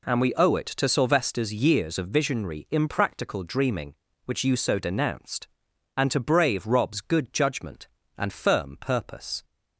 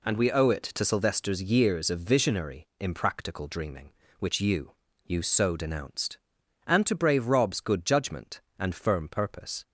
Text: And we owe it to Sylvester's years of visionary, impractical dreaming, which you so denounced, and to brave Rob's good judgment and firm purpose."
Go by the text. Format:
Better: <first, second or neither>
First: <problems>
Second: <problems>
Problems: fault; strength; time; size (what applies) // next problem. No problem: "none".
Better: first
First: none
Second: says "you" twice; at 5.0 s